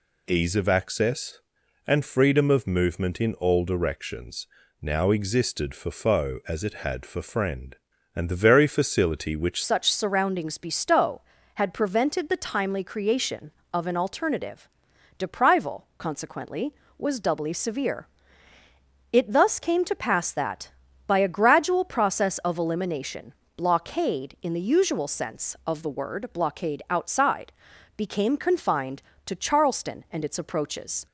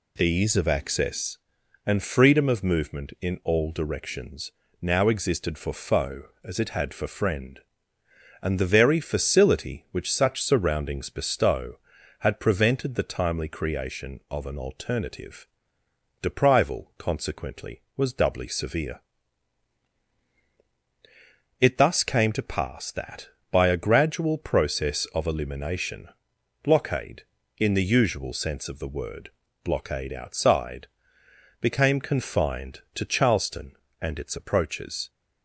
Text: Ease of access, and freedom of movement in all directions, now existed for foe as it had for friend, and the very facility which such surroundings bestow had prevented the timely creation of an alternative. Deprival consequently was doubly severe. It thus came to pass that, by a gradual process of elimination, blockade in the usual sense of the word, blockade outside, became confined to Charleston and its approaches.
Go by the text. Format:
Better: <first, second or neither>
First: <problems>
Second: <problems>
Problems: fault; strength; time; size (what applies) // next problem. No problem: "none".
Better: second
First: changes voice at "such"; from 9.6 s on; 21.4 s long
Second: none